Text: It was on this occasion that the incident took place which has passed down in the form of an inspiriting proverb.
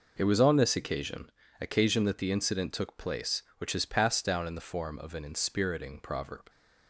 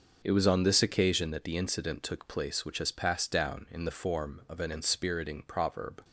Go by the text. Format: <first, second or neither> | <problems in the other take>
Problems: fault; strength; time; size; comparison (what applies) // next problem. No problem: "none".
second | says "occasion" twice; at 1.5 s